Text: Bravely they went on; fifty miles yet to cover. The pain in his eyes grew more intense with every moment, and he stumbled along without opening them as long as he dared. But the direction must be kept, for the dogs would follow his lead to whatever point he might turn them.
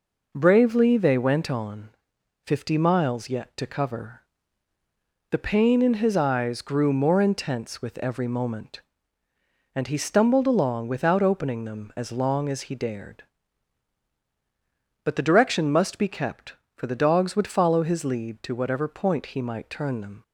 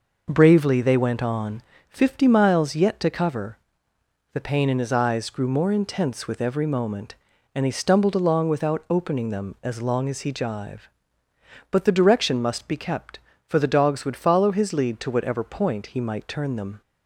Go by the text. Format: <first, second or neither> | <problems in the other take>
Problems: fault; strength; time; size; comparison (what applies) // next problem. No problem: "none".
first | says "jive" for "dared"; at 10.3 s